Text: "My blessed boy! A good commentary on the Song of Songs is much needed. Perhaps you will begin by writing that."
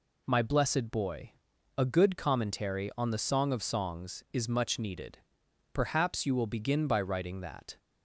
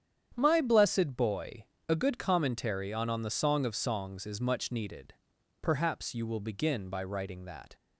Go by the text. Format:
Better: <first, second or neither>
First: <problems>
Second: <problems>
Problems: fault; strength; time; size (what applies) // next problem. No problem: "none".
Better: first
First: none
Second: starts louder than the rest; strong; until 1.3 s; 9 dB // says "on" twice; at 3.0 s